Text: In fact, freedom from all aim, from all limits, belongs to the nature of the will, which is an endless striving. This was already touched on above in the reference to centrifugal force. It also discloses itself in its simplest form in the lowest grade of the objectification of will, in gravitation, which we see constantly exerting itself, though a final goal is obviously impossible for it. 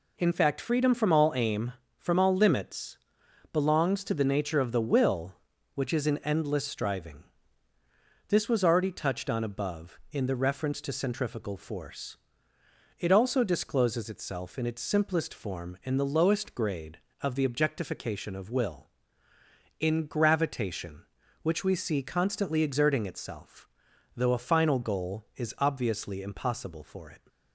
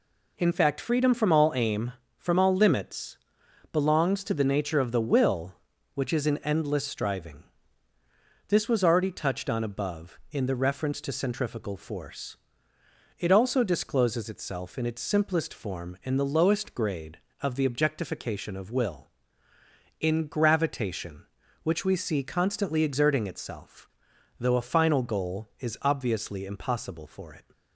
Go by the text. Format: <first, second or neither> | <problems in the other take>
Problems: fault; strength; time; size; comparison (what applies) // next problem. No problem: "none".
neither | none